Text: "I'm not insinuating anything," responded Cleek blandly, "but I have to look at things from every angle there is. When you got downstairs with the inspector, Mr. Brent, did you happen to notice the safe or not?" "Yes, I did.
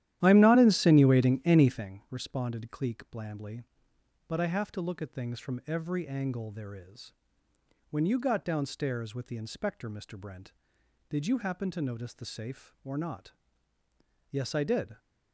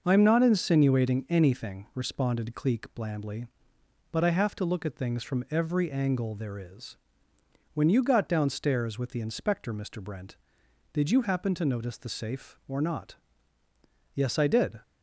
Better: second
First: starts louder than the rest; strong; until 1.9 s; 12.5 dB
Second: none

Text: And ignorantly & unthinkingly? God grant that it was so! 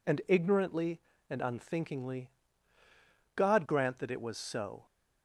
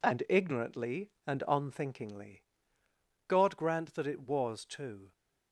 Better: first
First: none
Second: says "too" for "so"; at 4.6 s

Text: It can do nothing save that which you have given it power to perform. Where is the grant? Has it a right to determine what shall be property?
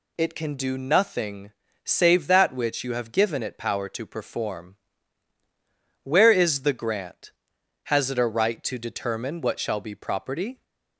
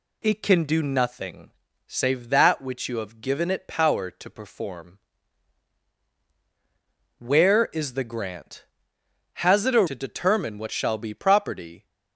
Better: first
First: pauses between "nothing" and "save"; slight; at 1.4 s; 0.34 s long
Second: pauses between "nothing" and "save"; slight; at 1.5 s; 0.34 s long // skips "right"; at 9.8 s

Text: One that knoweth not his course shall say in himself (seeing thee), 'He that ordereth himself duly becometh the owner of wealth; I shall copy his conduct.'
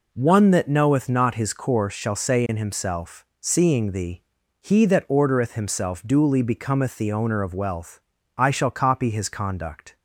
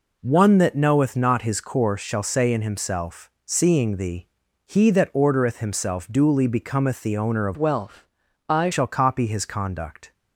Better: first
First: none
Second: changes voice from "wealth" to "I"; from 7.5 to 8.7 s; 1.2 s long

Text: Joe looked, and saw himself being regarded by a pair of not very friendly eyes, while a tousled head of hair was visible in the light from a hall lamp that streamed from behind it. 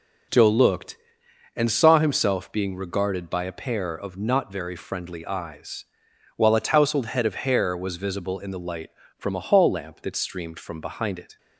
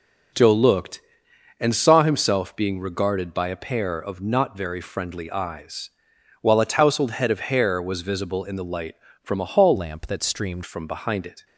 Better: first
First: none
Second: changes voice from "lamp" to "streamed"; from 9.7 to 10.6 s; 0.9 s long

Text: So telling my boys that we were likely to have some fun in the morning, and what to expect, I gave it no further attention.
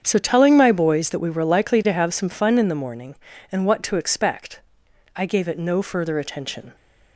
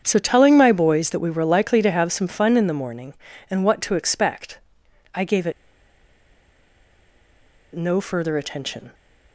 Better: first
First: starts louder than the rest; strong; until 1.0 s; 7.5 dB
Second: starts louder than the rest; strong; until 1.0 s; 7.5 dB // pauses between "it" and "no"; strong; at 5.5 s; 2.2 s long

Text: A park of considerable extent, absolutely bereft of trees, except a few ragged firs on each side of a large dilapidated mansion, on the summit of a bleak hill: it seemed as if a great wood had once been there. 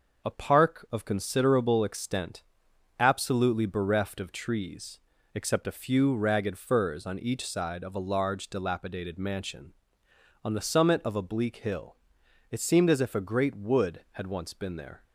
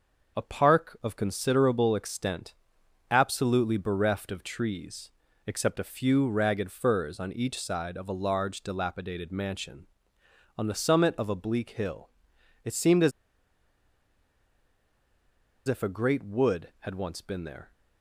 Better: first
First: none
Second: pauses between "as" and "if"; strong; at 13.1 s; 2.5 s long

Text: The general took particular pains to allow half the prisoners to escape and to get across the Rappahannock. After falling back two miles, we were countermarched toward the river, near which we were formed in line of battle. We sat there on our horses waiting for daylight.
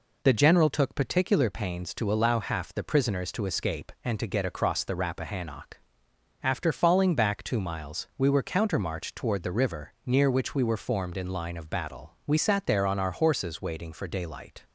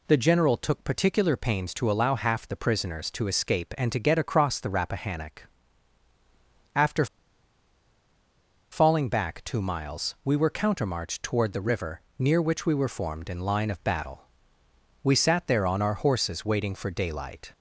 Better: first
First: none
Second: pauses between "After" and "falling"; strong; at 7.0 s; 1.6 s long

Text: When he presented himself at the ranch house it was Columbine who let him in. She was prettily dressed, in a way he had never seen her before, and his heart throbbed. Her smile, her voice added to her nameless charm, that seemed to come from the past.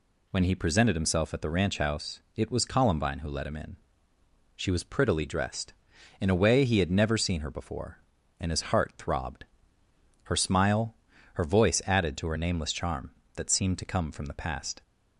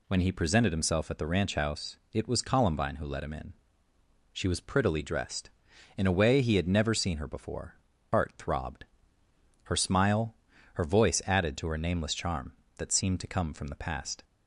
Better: first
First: pauses between "house" and "it"; slight; at 2.1 s; 0.16 s long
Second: pauses between "house" and "it"; slight; at 1.9 s; 0.16 s long // skips "and his"; at 7.9 s

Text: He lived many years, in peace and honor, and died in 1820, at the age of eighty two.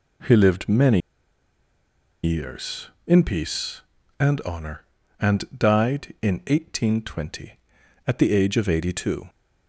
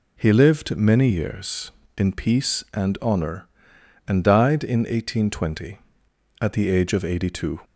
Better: second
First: pauses between "many" and "years"; at 0.9 s; 1.2 s long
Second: none

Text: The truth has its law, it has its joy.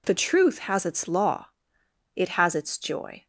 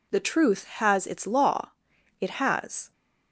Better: first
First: none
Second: stops before "its joy"; at 2.9 s

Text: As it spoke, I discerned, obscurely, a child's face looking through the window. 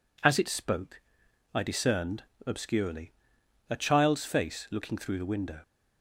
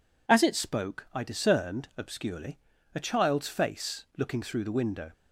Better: neither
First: none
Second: none

